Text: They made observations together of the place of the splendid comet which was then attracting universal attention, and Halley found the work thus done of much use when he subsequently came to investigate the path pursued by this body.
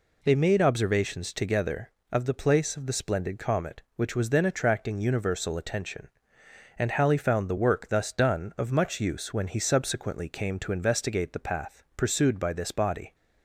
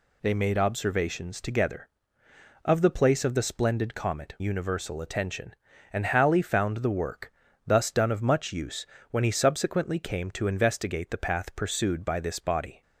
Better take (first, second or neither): first